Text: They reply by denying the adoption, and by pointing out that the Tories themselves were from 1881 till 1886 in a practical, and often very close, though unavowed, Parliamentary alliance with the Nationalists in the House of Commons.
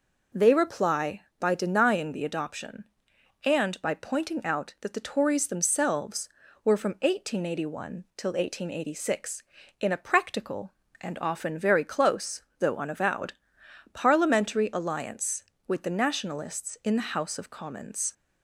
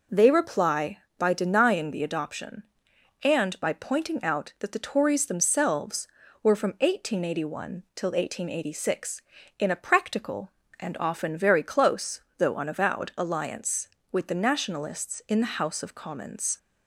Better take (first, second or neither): first